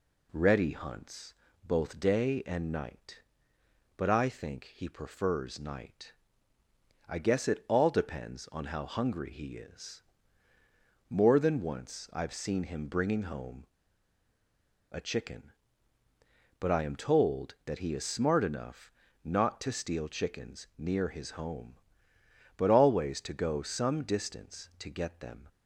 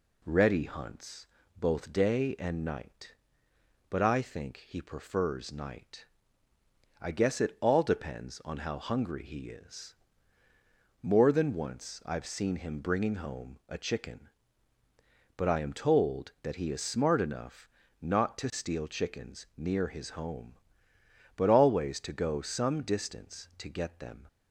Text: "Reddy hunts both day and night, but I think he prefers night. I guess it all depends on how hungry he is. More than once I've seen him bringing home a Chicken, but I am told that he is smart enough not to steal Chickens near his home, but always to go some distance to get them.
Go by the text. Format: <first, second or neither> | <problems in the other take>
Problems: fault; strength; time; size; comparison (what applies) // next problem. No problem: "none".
second | pauses between "hunts" and "both"; slight; at 1.3 s; 0.30 s long; slight in the second // pauses between "home" and "a"; strong; at 13.6 s; 1.2 s long // pauses between "enough" and "not"; slight; at 18.9 s; 0.32 s long; slight in the second